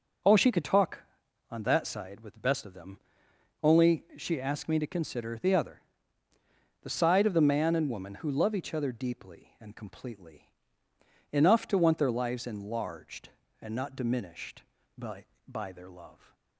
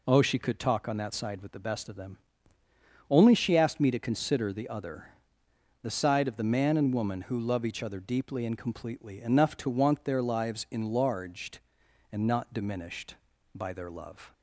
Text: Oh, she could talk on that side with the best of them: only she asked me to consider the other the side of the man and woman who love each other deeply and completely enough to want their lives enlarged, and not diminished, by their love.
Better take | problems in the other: second | pauses between "other" and "the"; at 5.7 s; 1.0 s long; noticeable in the second // pauses between "completely" and "enough"; noticeable; at 10.5 s; 0.80 s long // says "by" twice; at 15.4 s

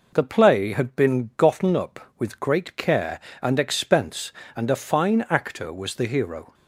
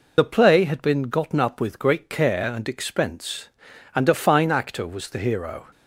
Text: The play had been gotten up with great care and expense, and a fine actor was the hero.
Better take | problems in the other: first | loses the start of "The"; at 0.1 s; 45 ms

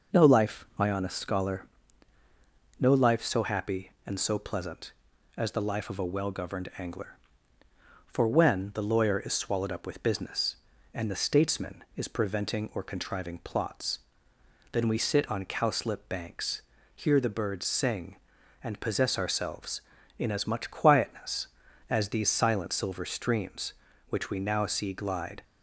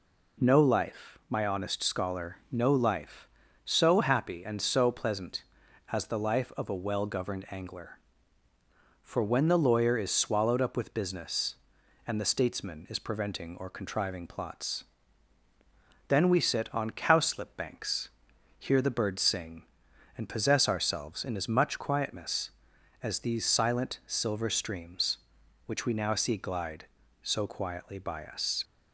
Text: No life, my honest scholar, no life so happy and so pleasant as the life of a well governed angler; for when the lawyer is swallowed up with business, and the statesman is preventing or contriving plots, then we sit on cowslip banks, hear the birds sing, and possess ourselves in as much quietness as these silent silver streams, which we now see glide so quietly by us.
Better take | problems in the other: second | stops before "so quietly by us"; at 25.4 s

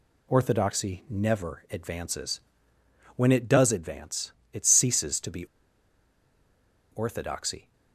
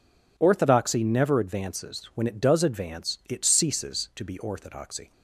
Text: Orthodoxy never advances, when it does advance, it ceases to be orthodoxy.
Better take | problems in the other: second | pauses between "be" and "orthodoxy"; strong; at 5.4 s; 1.4 s long

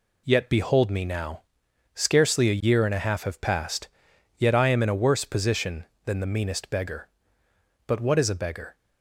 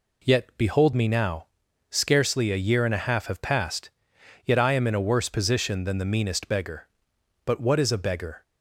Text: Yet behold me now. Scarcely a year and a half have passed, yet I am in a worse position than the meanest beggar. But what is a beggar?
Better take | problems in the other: neither | none

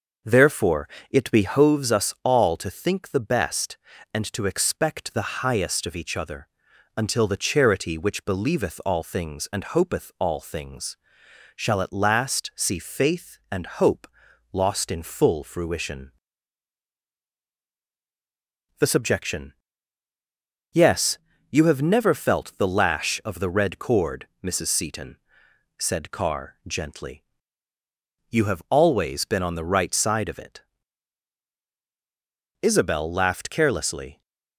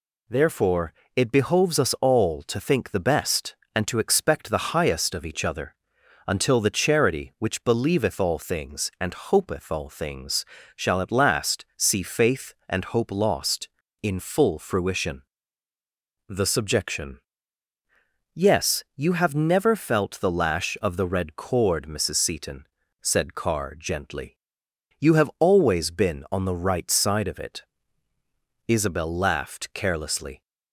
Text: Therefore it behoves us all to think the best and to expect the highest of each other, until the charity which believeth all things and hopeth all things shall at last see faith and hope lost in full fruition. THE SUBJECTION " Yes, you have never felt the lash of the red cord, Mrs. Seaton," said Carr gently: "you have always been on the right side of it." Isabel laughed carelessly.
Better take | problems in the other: second | starts louder than the rest; noticeable; until 1.9 s; 6 dB // pauses between "Therefore" and "it"; slight; at 0.8 s; 0.22 s long; slight in the second // pauses between "things" and "shall"; noticeable; at 10.9 s; 0.58 s long; slight in the second // pauses between "hope" and "lost"; noticeable; at 14.0 s; 0.46 s long

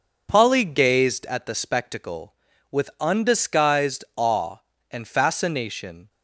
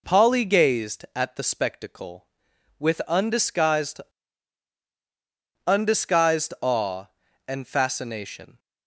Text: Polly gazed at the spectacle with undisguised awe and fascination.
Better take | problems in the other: first | says "undisguised" twice; at 5.6 s

